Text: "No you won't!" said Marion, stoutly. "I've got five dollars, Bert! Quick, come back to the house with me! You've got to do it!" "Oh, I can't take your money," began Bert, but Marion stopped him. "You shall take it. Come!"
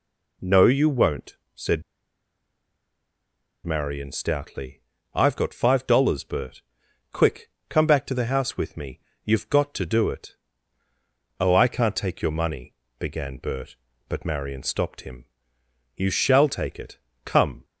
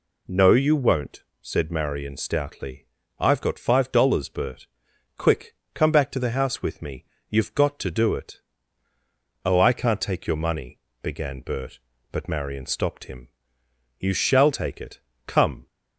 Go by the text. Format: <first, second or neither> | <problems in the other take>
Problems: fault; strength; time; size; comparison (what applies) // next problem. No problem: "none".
second | pauses between "said" and "Marion"; strong; at 1.8 s; 1.8 s long